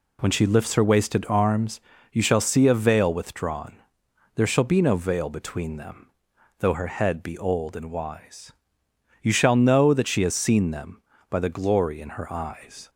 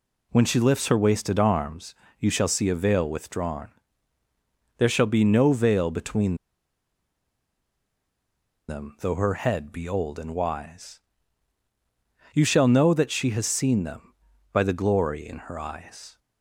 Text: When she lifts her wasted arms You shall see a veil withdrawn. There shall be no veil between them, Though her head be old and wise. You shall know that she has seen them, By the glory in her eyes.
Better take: first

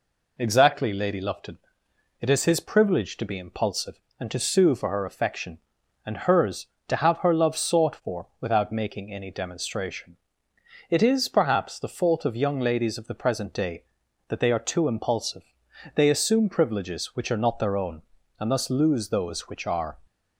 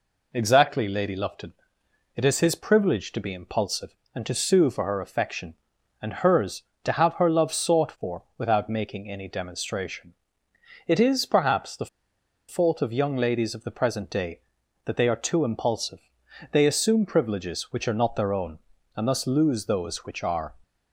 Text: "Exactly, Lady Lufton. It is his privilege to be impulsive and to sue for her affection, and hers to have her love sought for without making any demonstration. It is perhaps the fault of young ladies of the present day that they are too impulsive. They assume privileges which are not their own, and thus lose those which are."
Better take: first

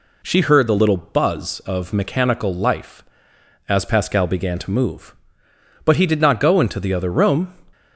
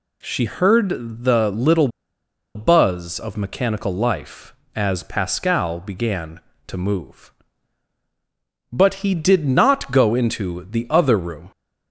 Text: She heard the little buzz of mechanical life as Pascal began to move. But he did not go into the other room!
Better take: first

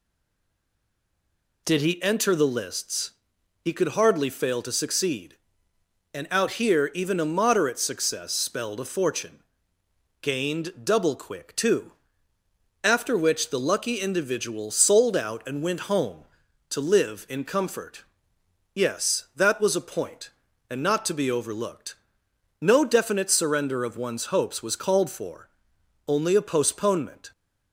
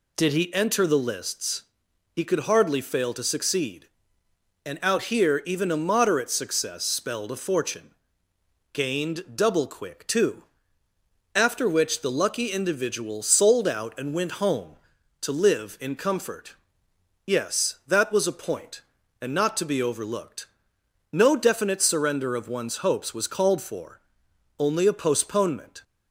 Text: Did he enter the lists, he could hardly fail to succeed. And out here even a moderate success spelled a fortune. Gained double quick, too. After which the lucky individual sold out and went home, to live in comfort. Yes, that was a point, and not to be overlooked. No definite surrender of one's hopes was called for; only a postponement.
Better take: second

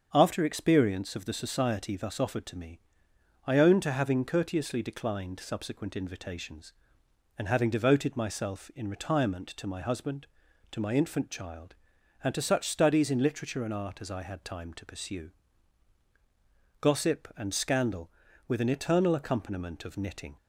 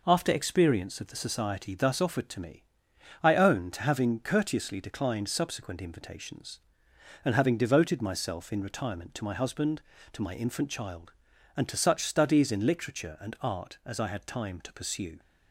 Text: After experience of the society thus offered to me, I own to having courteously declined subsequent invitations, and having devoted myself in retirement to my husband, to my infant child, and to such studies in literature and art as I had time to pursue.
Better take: second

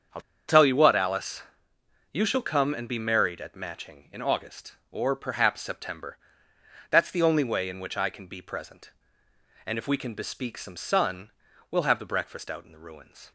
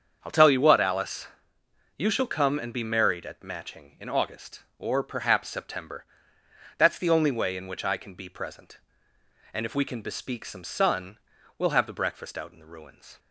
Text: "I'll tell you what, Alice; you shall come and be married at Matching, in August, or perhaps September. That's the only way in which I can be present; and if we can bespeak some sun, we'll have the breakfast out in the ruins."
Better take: second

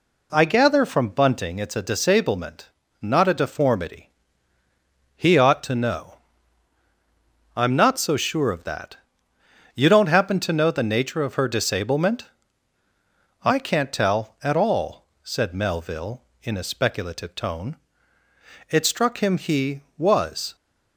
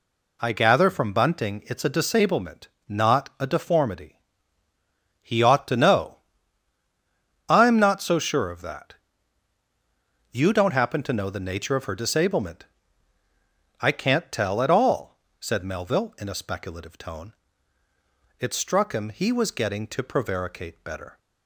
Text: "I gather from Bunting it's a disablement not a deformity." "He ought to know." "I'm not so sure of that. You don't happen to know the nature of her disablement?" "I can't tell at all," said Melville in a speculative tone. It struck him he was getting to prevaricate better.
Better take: second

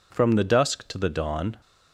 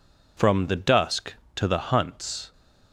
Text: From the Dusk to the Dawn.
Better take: first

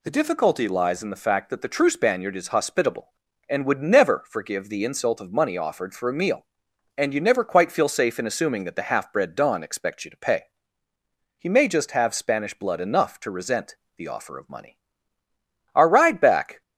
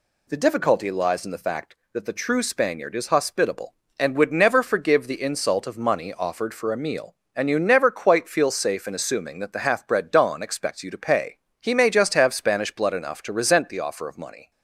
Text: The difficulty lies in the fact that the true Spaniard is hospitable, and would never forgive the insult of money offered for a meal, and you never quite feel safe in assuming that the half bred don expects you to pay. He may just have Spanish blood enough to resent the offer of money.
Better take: second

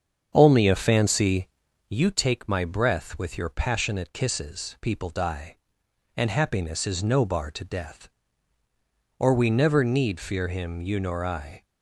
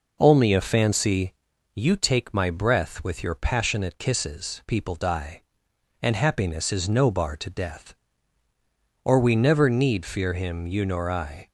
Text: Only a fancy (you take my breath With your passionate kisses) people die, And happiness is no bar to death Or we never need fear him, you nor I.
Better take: second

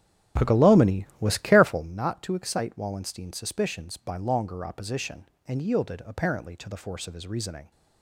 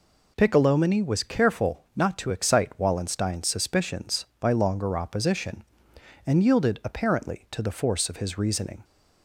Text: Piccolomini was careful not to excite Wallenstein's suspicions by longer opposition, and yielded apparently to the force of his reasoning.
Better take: second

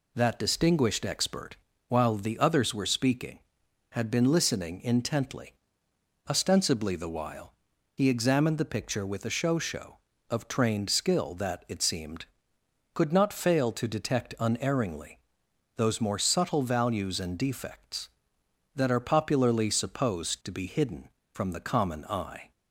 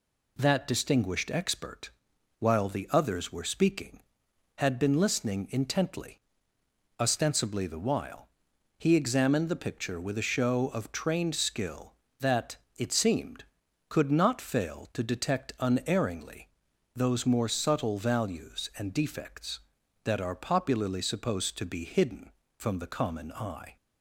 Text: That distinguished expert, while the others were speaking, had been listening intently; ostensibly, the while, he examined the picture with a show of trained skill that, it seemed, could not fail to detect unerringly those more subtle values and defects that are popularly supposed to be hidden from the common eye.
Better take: second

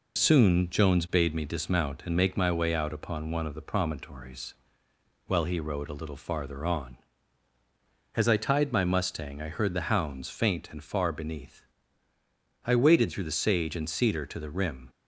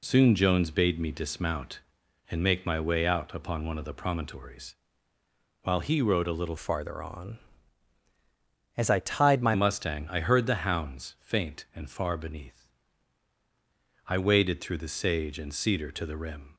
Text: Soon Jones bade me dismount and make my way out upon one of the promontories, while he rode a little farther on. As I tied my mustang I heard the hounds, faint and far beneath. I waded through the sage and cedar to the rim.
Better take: first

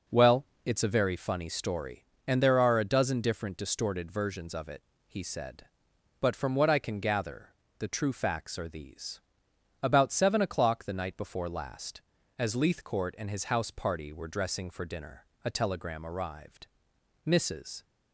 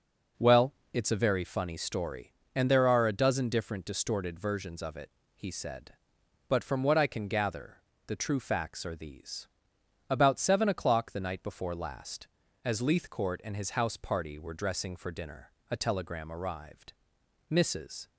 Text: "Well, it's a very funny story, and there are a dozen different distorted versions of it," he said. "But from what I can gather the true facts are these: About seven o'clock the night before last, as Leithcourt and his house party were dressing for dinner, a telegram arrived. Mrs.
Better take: neither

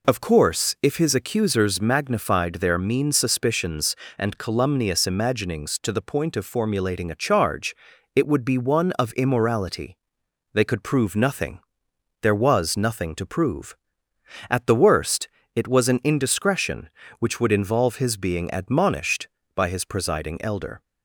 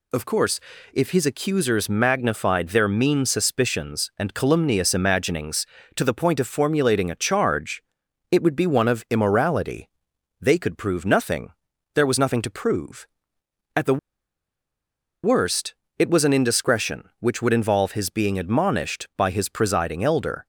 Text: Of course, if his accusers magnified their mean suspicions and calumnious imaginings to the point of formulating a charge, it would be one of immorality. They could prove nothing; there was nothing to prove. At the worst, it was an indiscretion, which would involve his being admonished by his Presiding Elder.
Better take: first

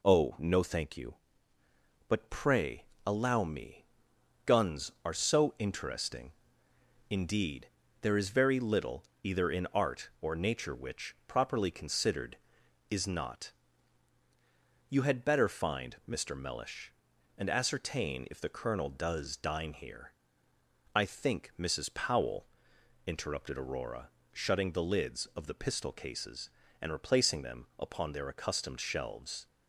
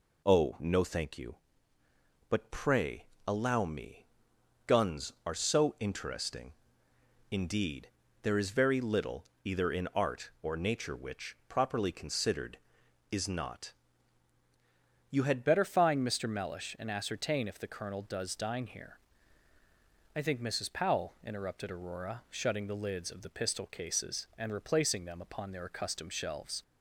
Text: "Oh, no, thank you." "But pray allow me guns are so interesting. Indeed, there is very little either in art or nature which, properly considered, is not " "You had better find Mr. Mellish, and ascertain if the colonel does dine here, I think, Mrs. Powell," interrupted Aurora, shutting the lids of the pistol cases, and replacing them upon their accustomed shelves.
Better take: first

